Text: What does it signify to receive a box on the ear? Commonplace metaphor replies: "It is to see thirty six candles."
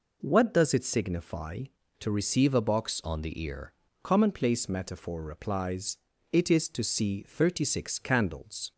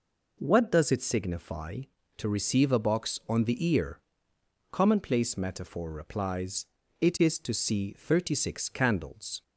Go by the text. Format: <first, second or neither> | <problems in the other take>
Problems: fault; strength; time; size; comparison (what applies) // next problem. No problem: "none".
second | changes voice from "on" to "ear"; from 3.0 to 3.7 s; 0.7 s long